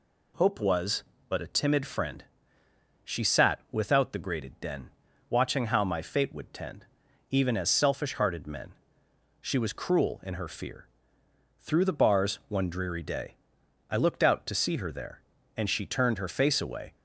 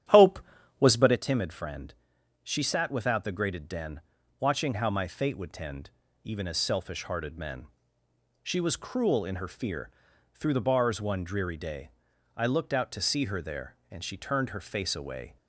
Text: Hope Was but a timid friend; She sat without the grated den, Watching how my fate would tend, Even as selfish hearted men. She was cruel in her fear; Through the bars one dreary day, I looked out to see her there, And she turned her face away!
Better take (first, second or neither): first